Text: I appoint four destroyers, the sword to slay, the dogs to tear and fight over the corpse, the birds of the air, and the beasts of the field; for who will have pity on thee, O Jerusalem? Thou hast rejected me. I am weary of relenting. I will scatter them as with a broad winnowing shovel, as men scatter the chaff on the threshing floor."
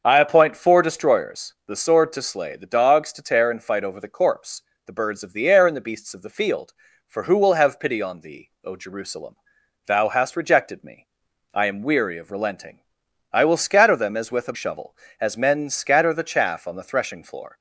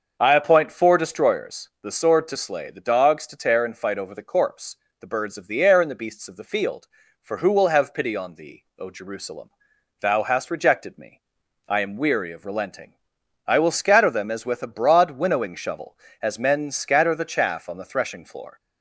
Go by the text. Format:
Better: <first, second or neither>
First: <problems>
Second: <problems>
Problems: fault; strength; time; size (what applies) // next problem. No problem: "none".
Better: second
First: starts louder than the rest; until 1.0 s; 6.5 dB // skips "broad winnowing"; at 14.5 s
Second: starts louder than the rest; until 1.2 s; 6.5 dB